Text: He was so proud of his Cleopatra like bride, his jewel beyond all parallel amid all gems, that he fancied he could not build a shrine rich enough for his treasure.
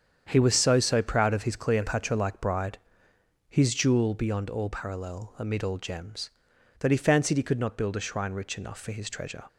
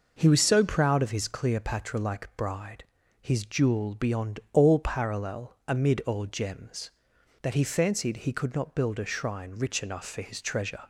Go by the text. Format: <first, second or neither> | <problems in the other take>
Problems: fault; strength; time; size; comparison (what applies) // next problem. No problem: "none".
second | starts louder than the rest; strong; until 1.2 s; 8 dB // says "so" twice; at 0.7 s